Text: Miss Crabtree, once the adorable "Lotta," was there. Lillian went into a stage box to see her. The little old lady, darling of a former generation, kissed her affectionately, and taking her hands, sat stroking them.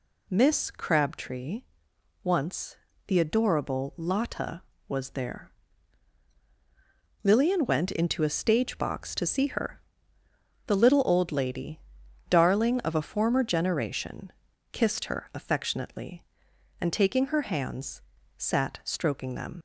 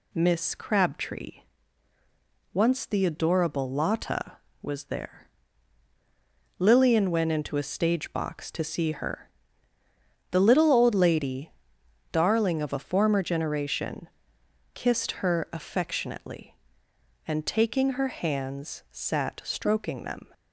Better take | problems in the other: second | pauses between "once" and "the"; slight; at 2.7 s; 0.32 s long // leaves "them" unfinished; at 19.5 s; 60 ms

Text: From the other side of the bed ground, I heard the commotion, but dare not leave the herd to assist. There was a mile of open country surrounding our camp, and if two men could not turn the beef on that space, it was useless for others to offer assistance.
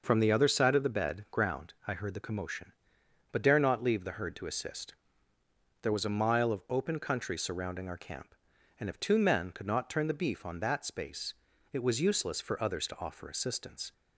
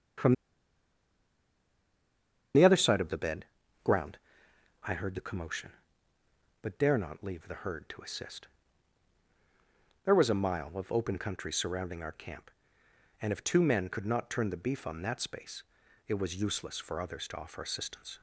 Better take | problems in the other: first | starts louder than the rest; strong; until 3.3 s; 7.5 dB // pauses between "From" and "the"; strong; at 0.3 s; 2.2 s long // pauses between "bed" and "ground"; slight; at 3.4 s; 0.36 s long

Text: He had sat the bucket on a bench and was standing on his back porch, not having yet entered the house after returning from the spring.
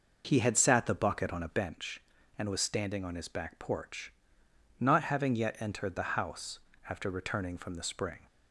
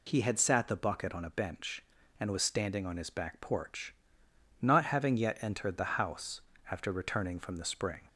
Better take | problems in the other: second | starts louder than the rest; noticeable; until 1.8 s; 5.5 dB // pauses between "house" and "after"; slight; at 6.5 s; 0.32 s long; slight in the second

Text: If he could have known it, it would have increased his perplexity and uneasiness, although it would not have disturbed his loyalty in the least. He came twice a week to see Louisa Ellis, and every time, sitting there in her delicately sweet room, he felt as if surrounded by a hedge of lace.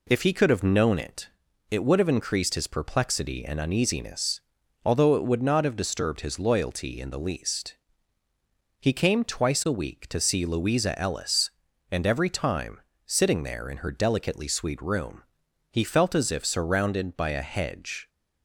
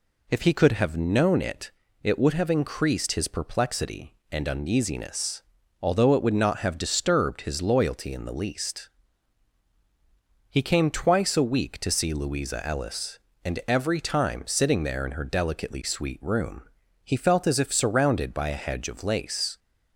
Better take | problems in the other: second | stops before "of lace"; at 18.0 s

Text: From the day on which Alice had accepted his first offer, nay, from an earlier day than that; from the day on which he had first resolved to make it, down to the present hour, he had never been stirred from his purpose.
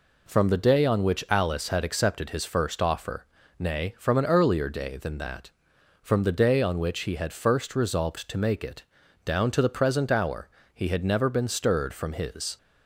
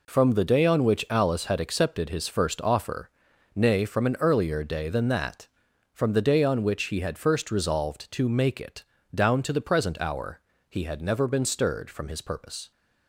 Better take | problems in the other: second | stops before "purpose"; at 12.5 s

